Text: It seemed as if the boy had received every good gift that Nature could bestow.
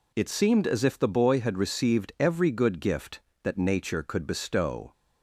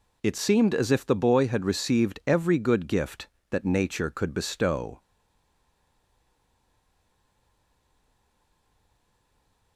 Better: first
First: none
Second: stays silent after the last word; strong; from 4.9 s on; 4.8 s long

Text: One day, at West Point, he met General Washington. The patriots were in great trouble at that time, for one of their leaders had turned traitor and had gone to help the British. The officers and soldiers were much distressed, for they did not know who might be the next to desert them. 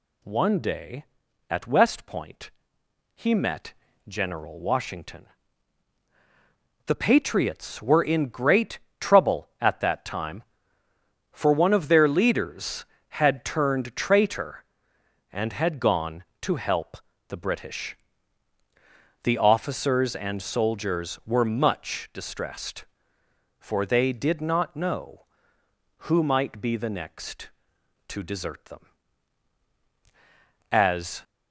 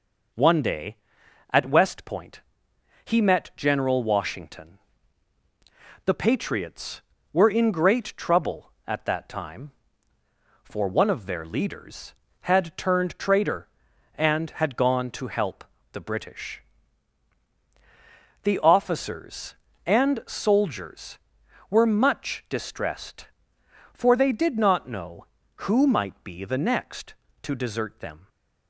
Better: second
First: pauses between "met" and "General"; slight; at 3.7 s; 0.34 s long // pauses between "great" and "trouble"; slight; at 8.7 s; 0.22 s long // pauses between "help" and "the"; slight; at 16.9 s; 0.30 s long // goes on to say "As"; from 30.7 s on; 0.52 s long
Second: pauses between "help" and "the"; slight; at 15.6 s; 0.28 s long

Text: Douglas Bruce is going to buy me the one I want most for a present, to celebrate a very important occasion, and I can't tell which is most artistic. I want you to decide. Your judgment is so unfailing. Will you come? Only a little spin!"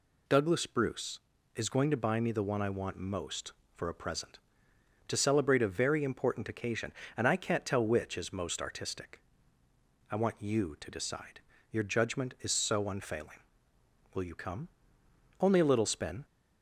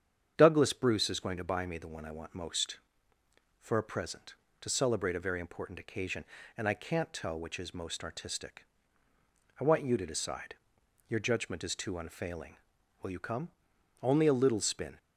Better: first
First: none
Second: starts louder than the rest; strong; until 1.3 s; 8 dB // says "too" for "so"; at 11.7 s

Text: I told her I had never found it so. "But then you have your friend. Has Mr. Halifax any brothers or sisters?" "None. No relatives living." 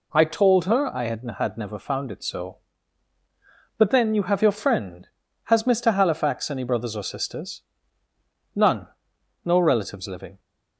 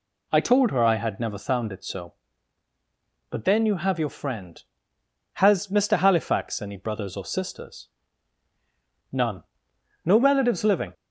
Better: second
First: says "had" twice; at 1.3 s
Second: none

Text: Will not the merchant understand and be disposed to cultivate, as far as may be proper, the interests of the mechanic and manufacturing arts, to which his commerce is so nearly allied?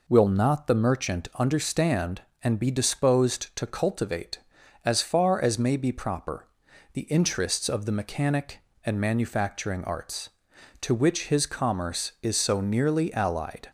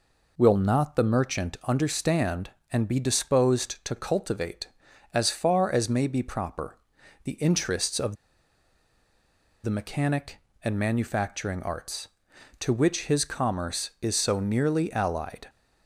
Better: first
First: none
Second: pauses between "of" and "the"; strong; at 8.1 s; 1.4 s long

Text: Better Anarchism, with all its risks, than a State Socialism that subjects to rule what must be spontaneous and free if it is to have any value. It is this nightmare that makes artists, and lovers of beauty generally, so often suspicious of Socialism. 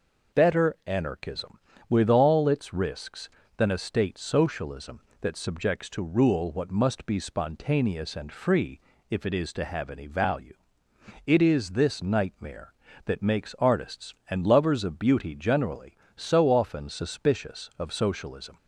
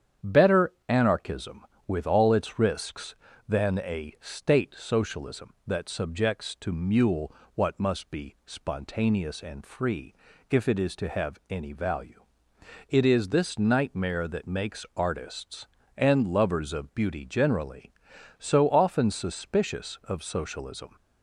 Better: first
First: pauses between "free" and "if"; slight; at 8.8 s; 0.30 s long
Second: starts louder than the rest; strong; until 1.4 s; 9 dB // pauses between "Better" and "Anarchism"; slight; at 0.7 s; 0.16 s long // says "mule" for "rule"; at 6.7 s // pauses between "free" and "if"; slight; at 10.1 s; 0.36 s long

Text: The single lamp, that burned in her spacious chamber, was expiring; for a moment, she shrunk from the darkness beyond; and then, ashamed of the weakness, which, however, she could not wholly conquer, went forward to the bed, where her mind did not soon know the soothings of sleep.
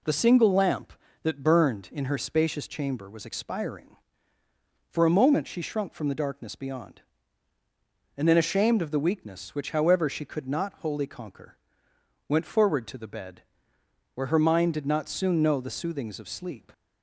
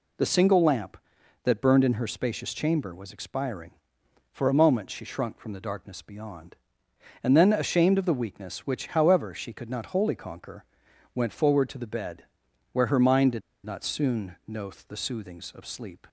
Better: first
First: none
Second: pauses between "did" and "not"; slight; at 13.4 s; 0.25 s long // pauses between "know" and "the"; slight; at 14.7 s; 0.16 s long

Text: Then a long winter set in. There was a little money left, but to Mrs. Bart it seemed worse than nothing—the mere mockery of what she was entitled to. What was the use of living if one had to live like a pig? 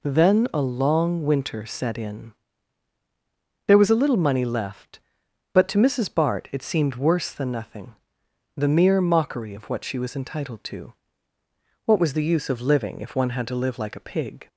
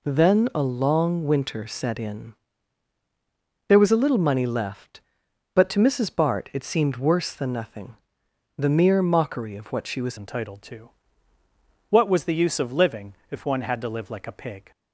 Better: first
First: none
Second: changes voice at "entitled"; from 10.1 s on; 4.6 s long // pauses between "living" and "if"; slight; at 13.1 s; 0.18 s long

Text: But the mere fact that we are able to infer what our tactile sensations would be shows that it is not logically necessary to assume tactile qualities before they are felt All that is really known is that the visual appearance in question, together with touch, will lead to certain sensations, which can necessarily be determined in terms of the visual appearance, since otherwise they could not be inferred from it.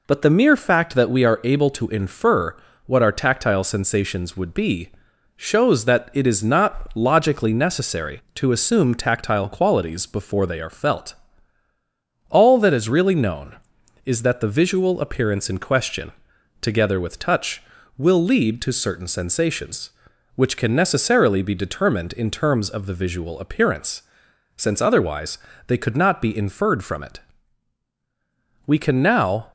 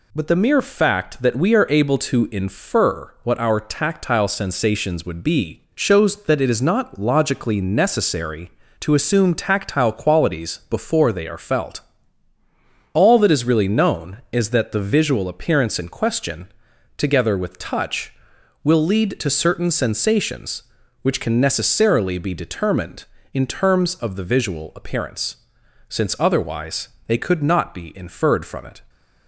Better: second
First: pauses between "infer" and "what"; slight; at 2.5 s; 0.30 s long // pauses between "be" and "shows"; at 4.9 s; 0.44 s long // pauses between "felt" and "All"; at 11.1 s; 1.1 s long // pauses between "otherwise" and "they"; slight; at 25.3 s; 0.30 s long // goes on to say "We can now"; noticeable; from 28.6 s on; 0.86 s long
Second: pauses between "felt" and "All"; at 11.8 s; 1.1 s long // pauses between "otherwise" and "they"; slight; at 26.8 s; 0.18 s long

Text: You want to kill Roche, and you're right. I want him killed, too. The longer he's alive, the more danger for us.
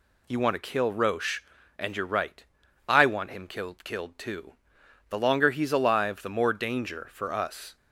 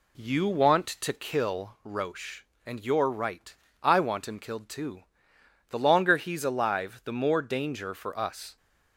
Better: second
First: says "killed" twice; at 3.8 s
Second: none

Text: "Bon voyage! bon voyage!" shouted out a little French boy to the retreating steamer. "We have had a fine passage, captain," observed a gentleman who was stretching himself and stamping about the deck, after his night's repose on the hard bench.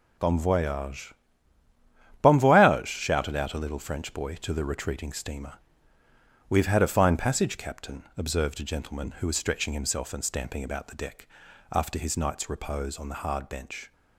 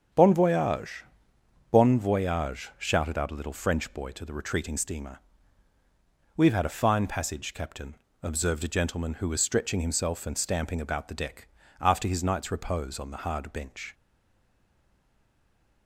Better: first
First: none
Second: starts louder than the rest; strong; until 1.7 s; 7.5 dB // stays silent after the last word; noticeable; from 13.9 s on; 1.9 s long

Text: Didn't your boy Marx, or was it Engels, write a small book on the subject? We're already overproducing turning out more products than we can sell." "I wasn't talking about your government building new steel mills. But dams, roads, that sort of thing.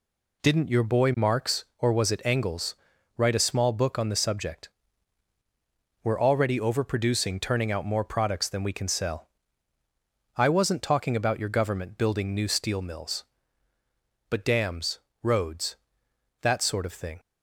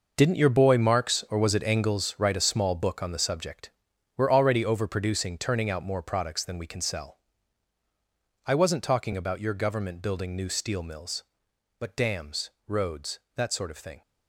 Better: first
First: none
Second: gets quieter; strong; throughout; 12 dB

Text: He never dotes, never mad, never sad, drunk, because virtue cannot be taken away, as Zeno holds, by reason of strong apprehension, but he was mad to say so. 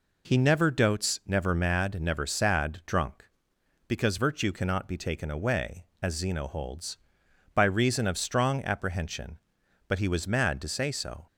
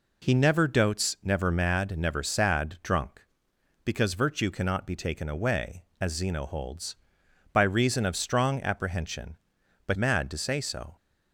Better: first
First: none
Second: skips "he was"; at 9.9 s

